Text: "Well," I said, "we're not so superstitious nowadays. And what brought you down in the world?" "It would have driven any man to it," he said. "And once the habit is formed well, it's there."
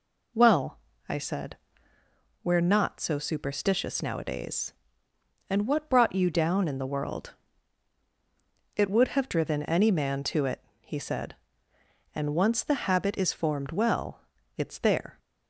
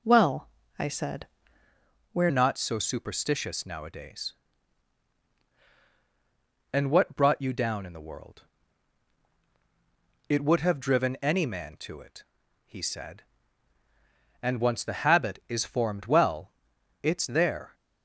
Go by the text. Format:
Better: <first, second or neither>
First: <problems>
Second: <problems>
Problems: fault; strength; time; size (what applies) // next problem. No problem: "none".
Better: first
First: none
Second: changes voice at "not"; from 2.2 s on; 15.5 s long